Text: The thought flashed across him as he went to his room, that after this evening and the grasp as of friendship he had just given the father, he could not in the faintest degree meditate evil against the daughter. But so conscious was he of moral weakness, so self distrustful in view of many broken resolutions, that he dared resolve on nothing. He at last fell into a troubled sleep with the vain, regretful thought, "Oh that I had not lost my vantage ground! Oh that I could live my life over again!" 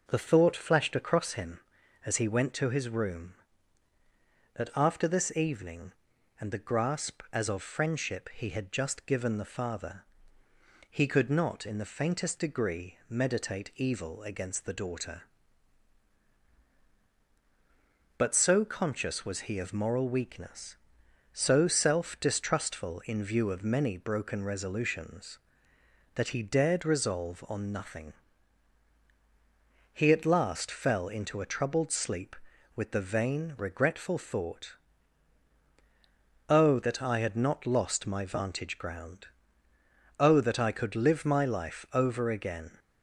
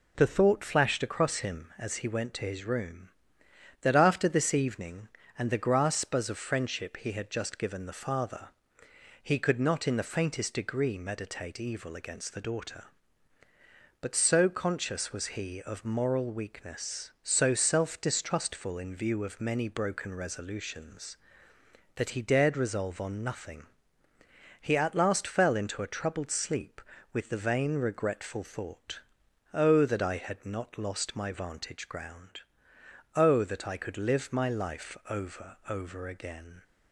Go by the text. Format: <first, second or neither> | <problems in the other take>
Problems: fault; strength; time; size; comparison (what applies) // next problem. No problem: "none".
first | says "over" twice; at 35.6 s